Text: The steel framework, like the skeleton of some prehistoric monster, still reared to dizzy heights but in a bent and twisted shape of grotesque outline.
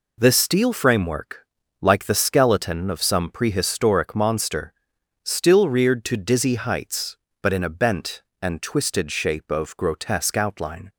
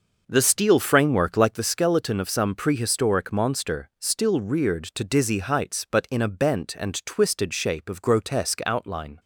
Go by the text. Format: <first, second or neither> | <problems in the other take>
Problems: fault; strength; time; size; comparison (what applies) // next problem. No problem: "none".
first | starts louder than the rest; noticeable; until 1.6 s; 6 dB